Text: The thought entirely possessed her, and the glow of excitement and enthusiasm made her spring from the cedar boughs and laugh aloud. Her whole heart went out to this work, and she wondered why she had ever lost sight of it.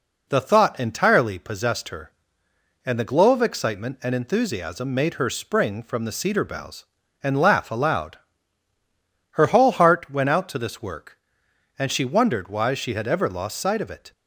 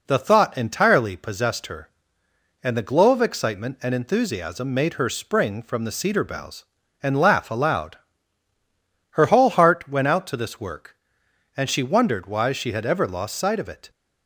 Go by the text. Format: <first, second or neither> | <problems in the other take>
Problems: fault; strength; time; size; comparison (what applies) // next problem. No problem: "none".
neither | none